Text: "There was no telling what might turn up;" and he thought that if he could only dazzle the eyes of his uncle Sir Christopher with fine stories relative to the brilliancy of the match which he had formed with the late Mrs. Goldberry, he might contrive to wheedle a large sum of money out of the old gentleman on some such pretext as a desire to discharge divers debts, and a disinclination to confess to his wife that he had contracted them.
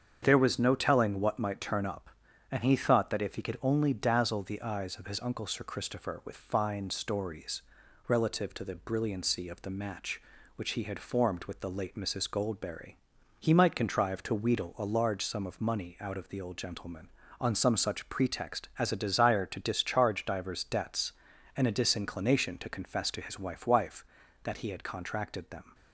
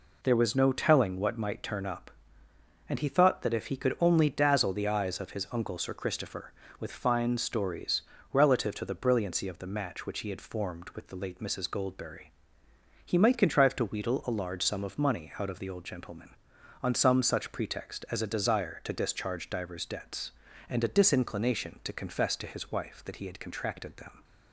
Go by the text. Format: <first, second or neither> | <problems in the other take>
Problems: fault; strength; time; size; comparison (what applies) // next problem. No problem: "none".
second | starts louder than the rest; strong; until 1.2 s; 7.5 dB // pauses between "stories" and "relative"; noticeable; at 7.6 s; 0.46 s long; slight in the second // says "wife" twice; at 23.6 s